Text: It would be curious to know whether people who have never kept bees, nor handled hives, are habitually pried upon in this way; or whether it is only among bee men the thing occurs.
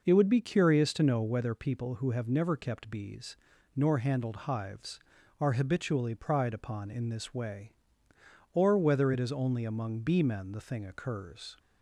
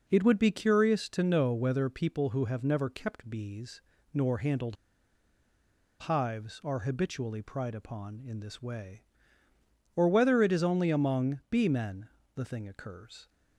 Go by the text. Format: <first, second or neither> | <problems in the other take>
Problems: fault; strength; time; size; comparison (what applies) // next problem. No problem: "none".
first | pauses between "handled" and "hives"; strong; at 4.7 s; 1.2 s long // pauses between "men" and "the"; slight; at 12.0 s; 0.26 s long